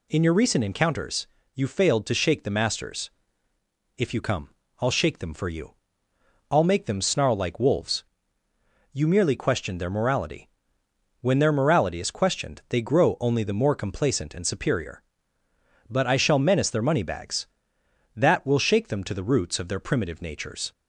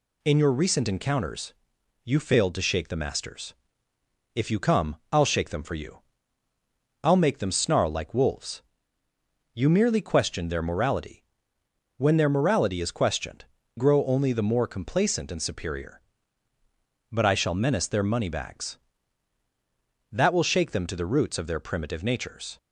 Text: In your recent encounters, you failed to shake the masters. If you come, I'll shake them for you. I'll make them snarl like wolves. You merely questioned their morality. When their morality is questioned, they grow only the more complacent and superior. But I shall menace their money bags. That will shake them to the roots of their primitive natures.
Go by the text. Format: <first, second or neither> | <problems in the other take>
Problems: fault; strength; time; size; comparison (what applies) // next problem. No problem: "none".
first | skips "they"; at 13.6 s